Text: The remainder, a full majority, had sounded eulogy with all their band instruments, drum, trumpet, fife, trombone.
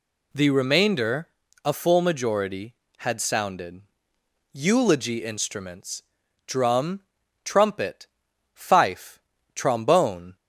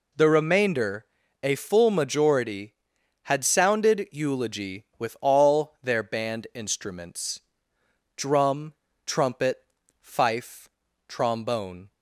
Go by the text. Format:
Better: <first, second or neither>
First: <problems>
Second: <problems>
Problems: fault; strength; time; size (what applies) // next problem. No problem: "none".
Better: second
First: pauses between "sounded" and "eulogy"; noticeable; at 3.8 s; 0.72 s long // skips "with all their band"; at 5.2 s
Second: none